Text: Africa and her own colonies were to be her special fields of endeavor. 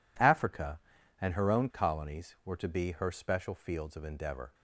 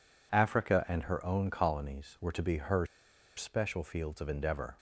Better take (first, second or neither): first